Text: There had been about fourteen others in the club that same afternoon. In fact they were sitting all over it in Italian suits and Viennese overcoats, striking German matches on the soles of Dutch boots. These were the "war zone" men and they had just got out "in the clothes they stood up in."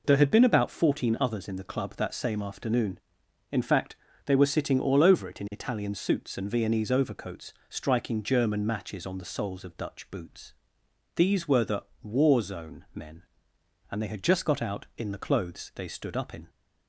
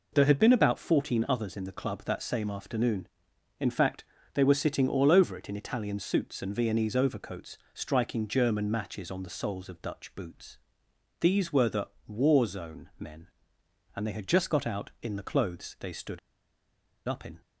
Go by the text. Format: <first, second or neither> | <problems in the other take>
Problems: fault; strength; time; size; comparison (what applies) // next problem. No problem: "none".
first | pauses between "fact" and "they"; slight; at 4.0 s; 0.30 s long; slight in the first // pauses between "the" and "war"; slight; at 11.8 s; 0.18 s long; slight in the first // pauses between "stood" and "up"; noticeable; at 16.1 s; 0.89 s long